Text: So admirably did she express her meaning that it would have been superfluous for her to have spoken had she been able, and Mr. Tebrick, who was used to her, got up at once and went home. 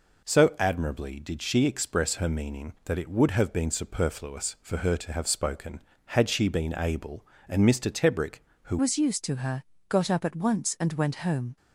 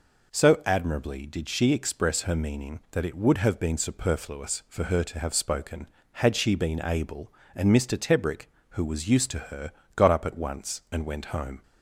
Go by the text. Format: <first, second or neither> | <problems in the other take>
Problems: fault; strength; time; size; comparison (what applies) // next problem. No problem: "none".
second | changes voice at "was"; from 8.7 s on; 2.8 s long